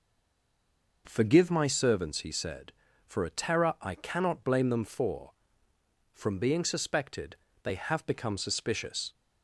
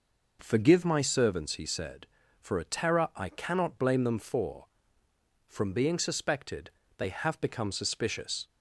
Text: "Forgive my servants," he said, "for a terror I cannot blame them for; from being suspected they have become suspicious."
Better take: second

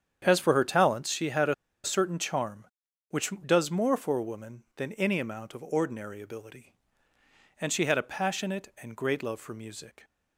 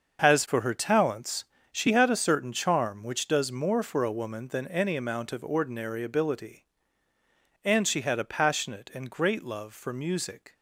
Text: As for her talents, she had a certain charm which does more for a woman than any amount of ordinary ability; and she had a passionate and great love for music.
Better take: second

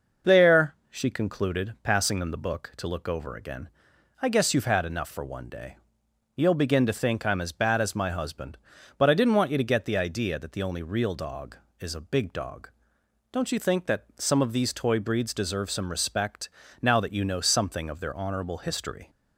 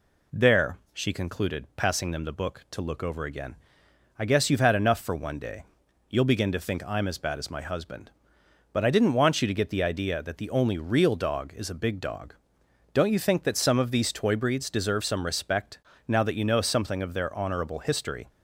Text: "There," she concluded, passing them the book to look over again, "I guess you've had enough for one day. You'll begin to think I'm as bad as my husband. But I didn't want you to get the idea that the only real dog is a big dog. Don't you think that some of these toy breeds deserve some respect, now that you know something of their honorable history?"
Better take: neither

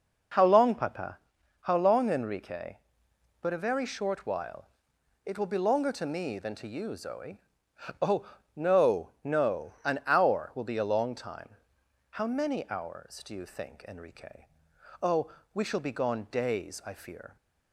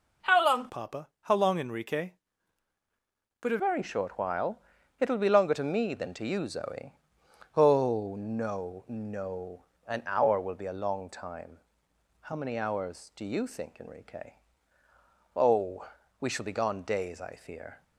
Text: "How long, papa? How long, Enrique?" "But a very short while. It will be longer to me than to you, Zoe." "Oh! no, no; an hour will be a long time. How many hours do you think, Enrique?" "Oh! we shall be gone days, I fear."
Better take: first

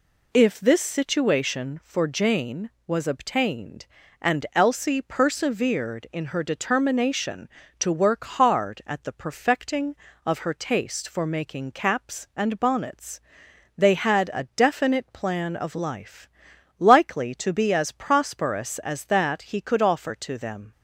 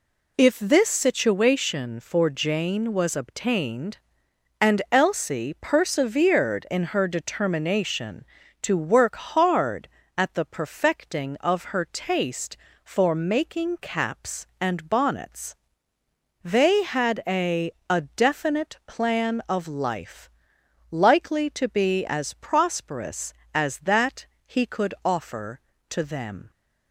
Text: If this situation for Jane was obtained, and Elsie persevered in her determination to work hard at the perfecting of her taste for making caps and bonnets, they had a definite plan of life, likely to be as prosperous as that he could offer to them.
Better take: first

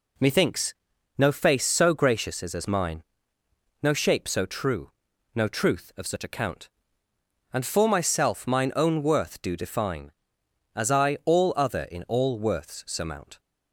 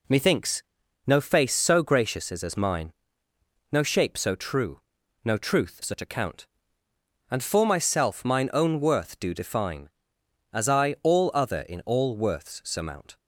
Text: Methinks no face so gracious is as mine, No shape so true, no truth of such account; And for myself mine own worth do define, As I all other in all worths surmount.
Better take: first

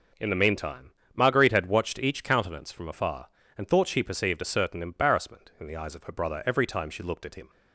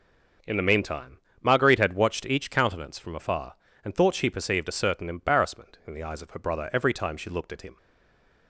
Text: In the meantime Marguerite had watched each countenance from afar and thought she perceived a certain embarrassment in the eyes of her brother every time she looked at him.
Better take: first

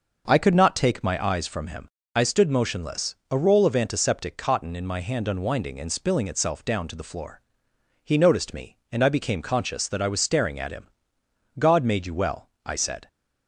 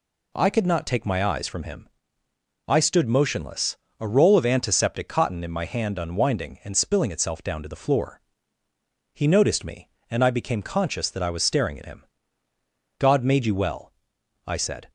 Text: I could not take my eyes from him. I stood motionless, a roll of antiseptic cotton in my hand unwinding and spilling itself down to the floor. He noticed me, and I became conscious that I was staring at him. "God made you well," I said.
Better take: neither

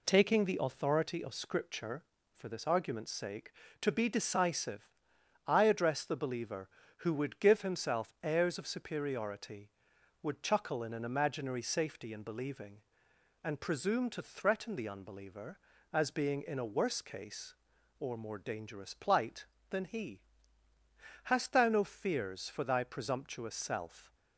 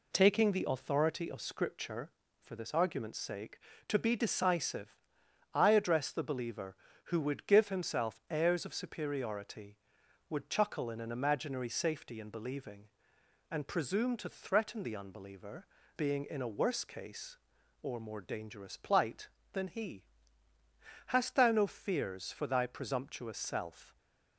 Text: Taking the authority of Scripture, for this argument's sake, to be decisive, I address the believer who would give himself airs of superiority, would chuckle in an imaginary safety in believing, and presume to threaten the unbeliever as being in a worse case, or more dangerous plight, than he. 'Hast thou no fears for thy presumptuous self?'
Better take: first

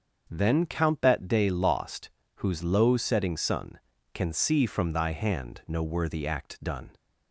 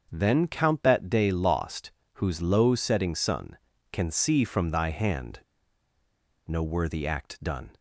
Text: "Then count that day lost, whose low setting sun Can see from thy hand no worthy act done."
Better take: first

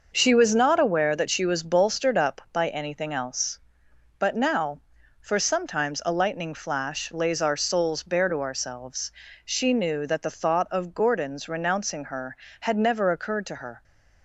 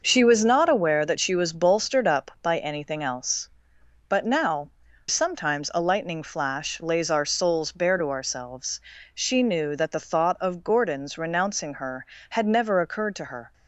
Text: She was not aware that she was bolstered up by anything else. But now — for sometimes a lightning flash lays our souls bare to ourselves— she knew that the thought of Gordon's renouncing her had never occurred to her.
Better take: first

